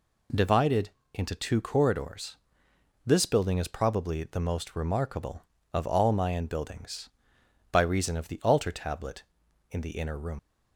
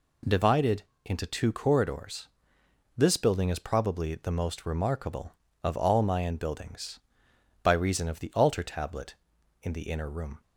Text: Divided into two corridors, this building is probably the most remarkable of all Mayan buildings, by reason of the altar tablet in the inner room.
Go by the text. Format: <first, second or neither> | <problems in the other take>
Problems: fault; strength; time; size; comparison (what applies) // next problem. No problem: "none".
second | pauses between "Divided" and "into"; slight; at 0.9 s; 0.22 s long; slight in the second // leaves "room" unfinished; at 10.3 s; 105 ms